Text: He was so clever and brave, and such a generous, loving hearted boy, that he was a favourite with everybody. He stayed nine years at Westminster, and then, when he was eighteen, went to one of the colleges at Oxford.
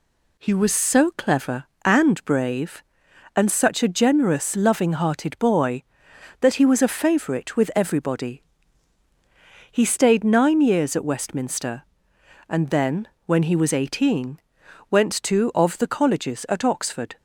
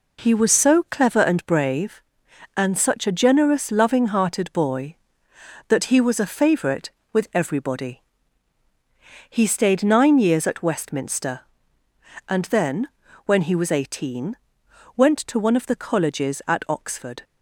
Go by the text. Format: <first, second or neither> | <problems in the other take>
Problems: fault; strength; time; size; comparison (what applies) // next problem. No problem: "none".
second | skips "one"; at 15.5 s